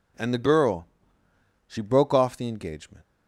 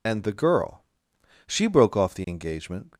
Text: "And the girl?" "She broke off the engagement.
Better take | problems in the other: first | loses the start of "And"; at 0.0 s; 70 ms

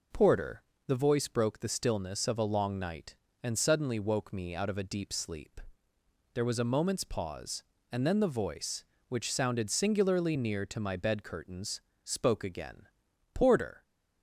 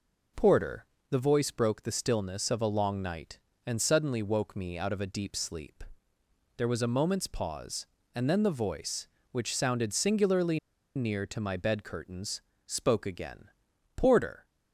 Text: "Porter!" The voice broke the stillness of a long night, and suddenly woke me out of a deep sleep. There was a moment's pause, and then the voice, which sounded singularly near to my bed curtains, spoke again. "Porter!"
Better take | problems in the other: first | pauses between "singularly" and "near"; at 10.5 s; 0.37 s long

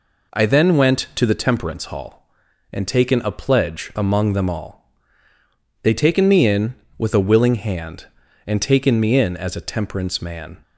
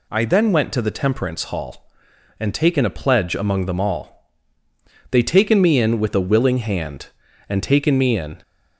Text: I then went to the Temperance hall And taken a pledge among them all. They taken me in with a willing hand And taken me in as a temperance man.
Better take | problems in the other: first | stops before "as a temperance man"; at 8.4 s

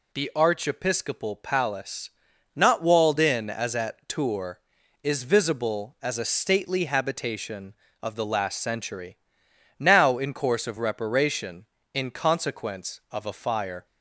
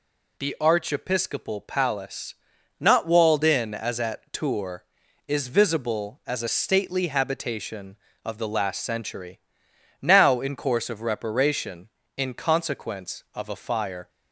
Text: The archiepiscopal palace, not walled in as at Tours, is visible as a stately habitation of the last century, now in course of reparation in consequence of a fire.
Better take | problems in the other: neither | none

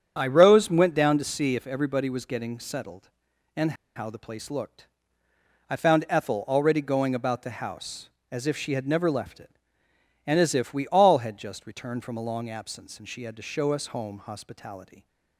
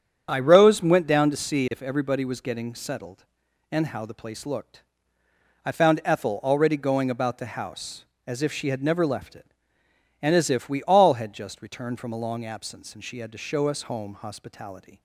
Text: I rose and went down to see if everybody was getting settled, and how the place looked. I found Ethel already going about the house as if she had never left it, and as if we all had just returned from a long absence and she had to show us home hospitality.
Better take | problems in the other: second | starts louder than the rest; strong; until 1.1 s; 8 dB; strong in the second // pauses between "and" and "how"; slight; at 3.7 s; 0.22 s long

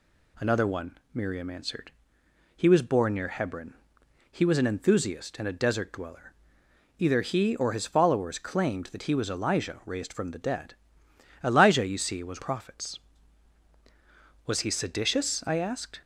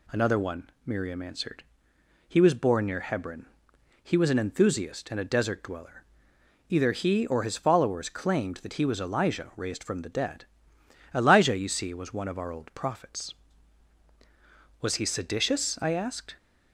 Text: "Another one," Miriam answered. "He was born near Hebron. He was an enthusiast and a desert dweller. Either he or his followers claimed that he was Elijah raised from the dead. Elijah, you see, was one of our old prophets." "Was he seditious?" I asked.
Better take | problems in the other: second | skips "one of our old"; at 12.4 s

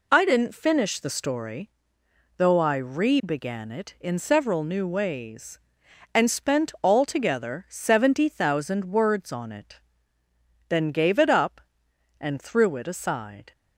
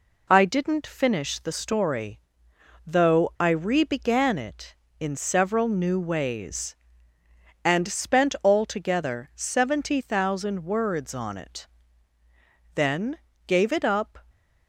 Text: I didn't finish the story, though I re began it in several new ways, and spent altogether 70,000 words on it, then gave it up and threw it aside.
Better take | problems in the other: first | pauses between "then" and "gave"; slight; at 13.1 s; 0.28 s long // stops before "and threw it aside"; at 14.2 s

